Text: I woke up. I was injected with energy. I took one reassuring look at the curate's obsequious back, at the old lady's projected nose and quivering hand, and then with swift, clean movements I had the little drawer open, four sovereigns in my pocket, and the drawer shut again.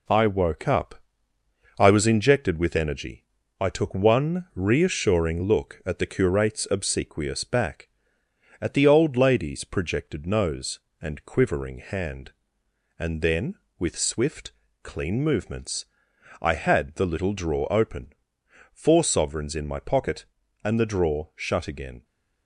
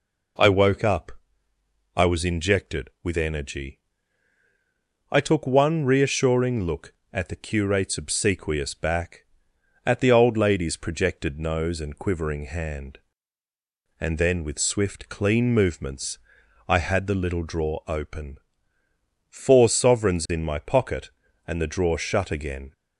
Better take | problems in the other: second | gets quieter; noticeable; throughout; 4.5 dB // pauses between "movements" and "I"; noticeable; at 15.8 s; 0.56 s long; noticeable in the second

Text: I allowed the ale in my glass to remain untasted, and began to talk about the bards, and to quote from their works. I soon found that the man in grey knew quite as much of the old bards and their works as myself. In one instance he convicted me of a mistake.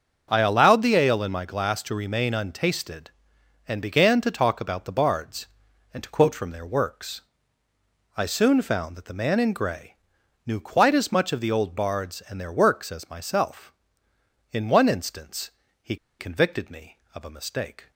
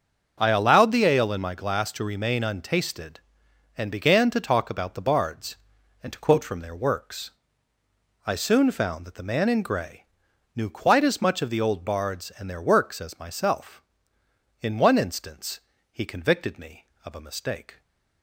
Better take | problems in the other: second | starts louder than the rest; until 1.3 s; 6.5 dB; also in the second // pauses between "grey" and "knew"; noticeable; at 9.9 s; 0.50 s long; noticeable in the second // pauses between "instance" and "he"; slight; at 15.4 s; 0.32 s long; slight in the second // pauses between "he" and "convicted"; slight; at 15.9 s; 0.24 s long

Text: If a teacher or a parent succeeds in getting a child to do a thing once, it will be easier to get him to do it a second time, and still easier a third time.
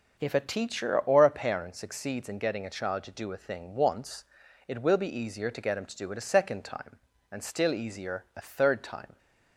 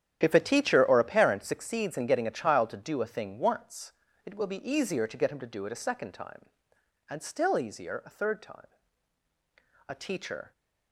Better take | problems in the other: first | starts louder than the rest; strong; until 1.2 s; 10 dB // goes on to say "A teacher"; noticeable; from 9.8 s on; 0.64 s long

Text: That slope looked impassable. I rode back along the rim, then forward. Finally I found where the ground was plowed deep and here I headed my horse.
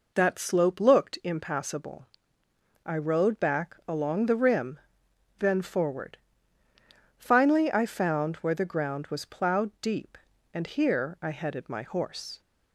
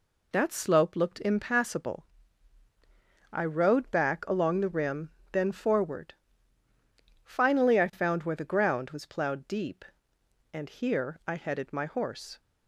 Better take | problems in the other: neither | none

